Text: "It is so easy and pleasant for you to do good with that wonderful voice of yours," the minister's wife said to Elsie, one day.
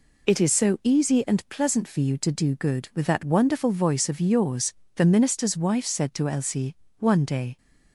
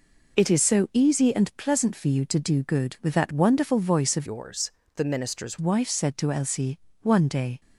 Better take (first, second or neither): first